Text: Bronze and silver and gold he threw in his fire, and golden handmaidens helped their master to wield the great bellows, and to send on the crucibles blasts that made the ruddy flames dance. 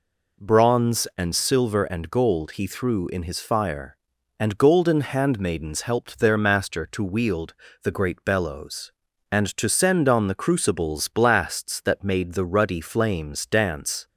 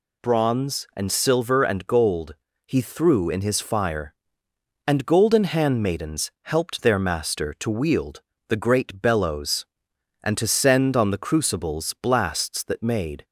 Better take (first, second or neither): first